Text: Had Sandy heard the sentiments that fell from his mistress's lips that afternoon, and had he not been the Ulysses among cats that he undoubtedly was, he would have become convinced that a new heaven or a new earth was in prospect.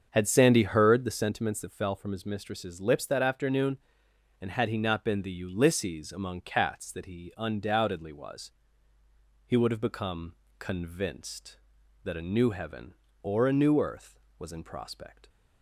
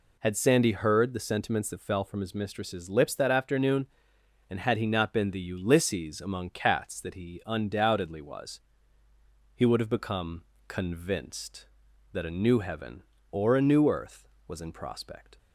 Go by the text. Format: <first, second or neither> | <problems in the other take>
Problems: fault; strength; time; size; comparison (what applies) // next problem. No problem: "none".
second | starts louder than the rest; until 1.4 s; 7 dB // pauses between "become" and "convinced"; slight; at 10.3 s; 0.24 s long; slight in the second